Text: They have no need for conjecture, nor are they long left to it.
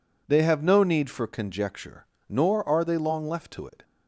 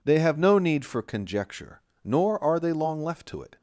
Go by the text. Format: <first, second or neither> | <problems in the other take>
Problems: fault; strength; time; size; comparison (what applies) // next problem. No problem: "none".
neither | none